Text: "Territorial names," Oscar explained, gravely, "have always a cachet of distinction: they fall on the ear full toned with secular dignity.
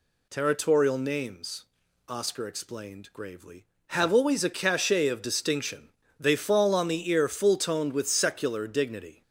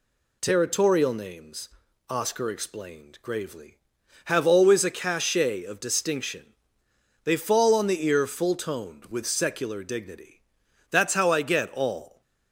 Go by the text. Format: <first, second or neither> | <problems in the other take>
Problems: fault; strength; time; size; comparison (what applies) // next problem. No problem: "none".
first | goes on to say "That's how I get all"; noticeable; from 10.9 s on; 1.3 s long